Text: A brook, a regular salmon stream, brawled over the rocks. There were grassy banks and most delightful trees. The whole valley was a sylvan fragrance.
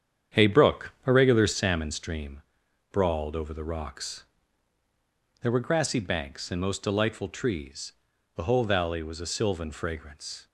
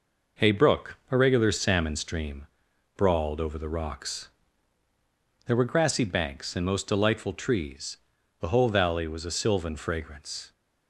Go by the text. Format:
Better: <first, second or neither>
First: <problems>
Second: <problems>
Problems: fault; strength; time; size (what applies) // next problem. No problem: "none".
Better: second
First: starts louder than the rest; strong; until 1.6 s; 8.5 dB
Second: none